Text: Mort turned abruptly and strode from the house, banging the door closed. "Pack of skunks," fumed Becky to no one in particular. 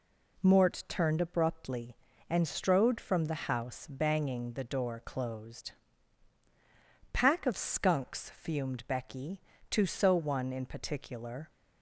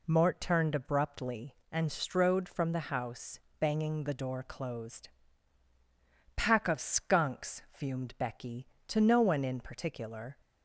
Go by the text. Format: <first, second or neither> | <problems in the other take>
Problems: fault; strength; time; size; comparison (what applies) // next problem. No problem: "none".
second | says "so" for "no"; at 9.8 s